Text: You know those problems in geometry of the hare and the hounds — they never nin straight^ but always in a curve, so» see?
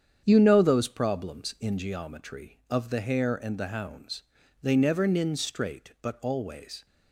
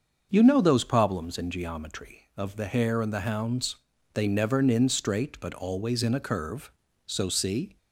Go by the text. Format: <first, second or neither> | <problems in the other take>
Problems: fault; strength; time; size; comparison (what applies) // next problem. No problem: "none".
second | starts louder than the rest; strong; until 1.2 s; 8 dB; also in the second // stops before "in a curve so see"; at 6.8 s